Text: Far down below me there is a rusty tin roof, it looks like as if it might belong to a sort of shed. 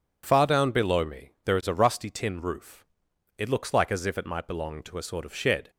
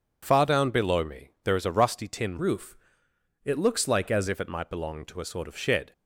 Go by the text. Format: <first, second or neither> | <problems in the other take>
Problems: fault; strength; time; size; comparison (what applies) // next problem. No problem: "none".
first | changes voice from "roof" to "as"; from 2.3 to 4.2 s; 1.9 s long